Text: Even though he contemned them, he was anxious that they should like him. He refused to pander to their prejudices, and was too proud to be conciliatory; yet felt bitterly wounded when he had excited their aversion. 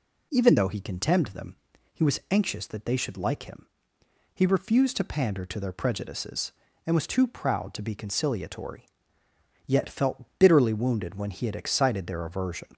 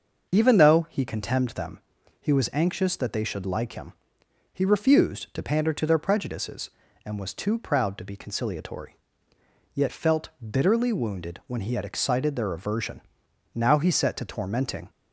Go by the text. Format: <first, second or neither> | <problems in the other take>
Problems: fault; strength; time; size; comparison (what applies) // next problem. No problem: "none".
first | starts louder than the rest; until 1.3 s; 6.5 dB // pauses between "felt" and "bitterly"; slight; at 10.2 s; 0.16 s long // goes on to say "Now he set to tormenting"; from 13.5 s on; 1.3 s long